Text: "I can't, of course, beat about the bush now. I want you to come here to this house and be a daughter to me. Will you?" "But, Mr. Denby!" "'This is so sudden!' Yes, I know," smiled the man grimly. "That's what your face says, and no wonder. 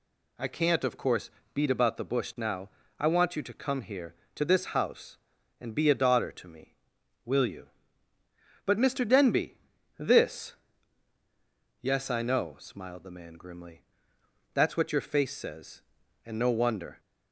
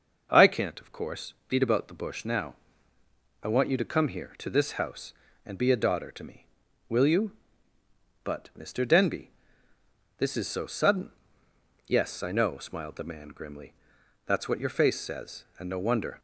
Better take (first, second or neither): second